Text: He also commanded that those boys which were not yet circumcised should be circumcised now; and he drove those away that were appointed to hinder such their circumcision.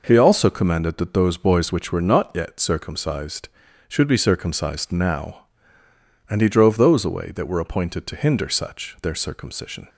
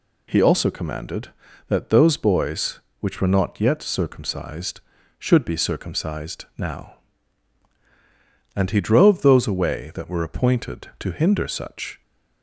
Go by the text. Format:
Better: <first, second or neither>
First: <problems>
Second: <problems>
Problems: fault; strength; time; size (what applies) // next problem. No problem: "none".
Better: first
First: none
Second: stops before "their circumcision"; at 12.0 s